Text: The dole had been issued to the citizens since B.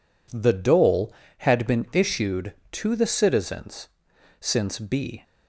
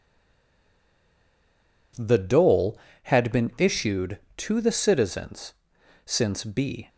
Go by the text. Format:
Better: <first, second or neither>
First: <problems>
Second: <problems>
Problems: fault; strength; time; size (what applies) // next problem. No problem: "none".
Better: first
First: pauses between "citizens" and "since"; noticeable; at 3.8 s; 0.50 s long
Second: stays silent before the first word; noticeable; until 1.9 s; 1.9 s long // pauses between "citizens" and "since"; noticeable; at 5.5 s; 0.50 s long